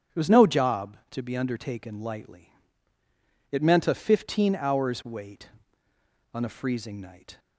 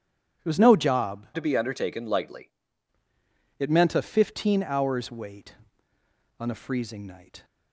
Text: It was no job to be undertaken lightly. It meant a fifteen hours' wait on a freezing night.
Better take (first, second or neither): first